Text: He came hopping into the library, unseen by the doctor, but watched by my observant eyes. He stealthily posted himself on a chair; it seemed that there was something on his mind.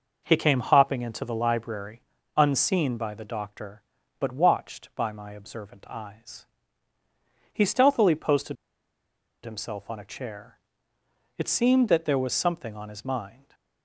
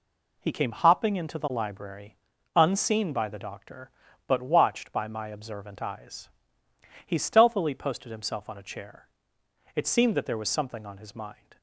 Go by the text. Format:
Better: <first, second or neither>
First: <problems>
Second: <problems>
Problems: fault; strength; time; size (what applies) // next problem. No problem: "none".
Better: second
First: pauses between "posted" and "himself"; noticeable; at 8.5 s; 0.88 s long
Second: none